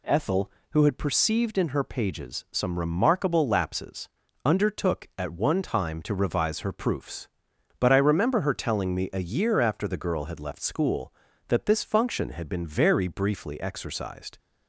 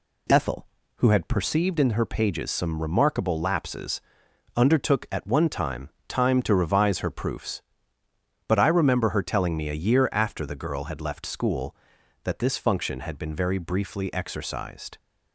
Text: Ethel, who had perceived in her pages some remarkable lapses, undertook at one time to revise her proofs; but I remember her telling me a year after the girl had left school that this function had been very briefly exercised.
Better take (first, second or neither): first